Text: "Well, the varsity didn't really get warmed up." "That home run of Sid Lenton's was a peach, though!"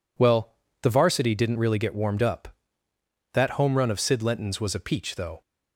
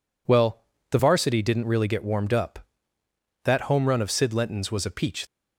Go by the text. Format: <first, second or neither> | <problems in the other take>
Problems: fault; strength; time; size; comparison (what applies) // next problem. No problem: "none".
first | stops before "though"; at 5.2 s